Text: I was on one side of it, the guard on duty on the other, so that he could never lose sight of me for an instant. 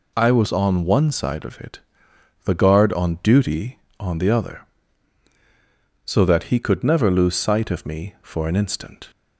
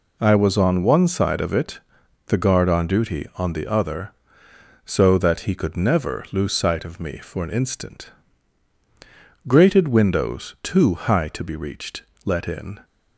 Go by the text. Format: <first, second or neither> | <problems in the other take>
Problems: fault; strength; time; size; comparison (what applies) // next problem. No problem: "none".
first | goes on to say "Grated windows too high to be reached let in"; strong; from 9.4 s on; 3.3 s long